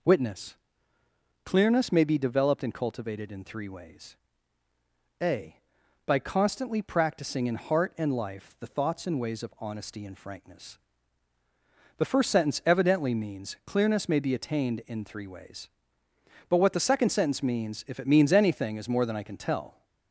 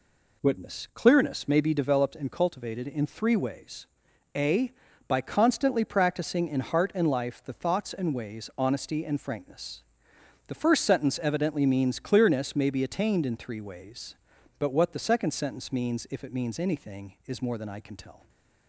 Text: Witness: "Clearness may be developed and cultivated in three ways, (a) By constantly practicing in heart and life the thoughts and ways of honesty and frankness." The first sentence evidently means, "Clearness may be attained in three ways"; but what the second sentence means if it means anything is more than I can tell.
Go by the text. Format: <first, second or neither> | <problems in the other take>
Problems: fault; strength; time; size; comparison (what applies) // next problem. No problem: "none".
first | skips "of"; at 8.5 s // stays silent after the last word; slight; from 18.1 s on; 0.5 s long